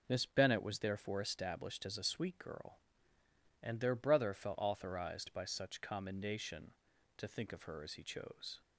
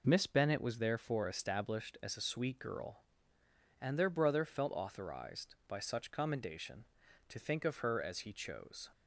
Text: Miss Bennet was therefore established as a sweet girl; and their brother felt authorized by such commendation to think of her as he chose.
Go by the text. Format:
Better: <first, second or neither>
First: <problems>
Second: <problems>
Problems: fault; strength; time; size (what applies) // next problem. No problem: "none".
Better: neither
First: none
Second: none